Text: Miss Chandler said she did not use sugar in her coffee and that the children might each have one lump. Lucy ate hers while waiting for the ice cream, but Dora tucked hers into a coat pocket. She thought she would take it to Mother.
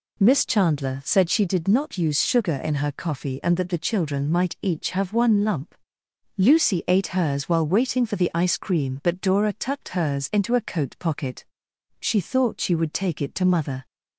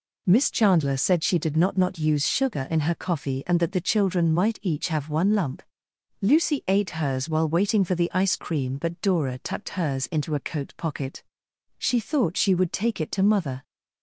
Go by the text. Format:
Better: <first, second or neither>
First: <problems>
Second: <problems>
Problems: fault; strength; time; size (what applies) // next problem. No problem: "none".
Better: first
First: none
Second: says "not" twice; at 1.7 s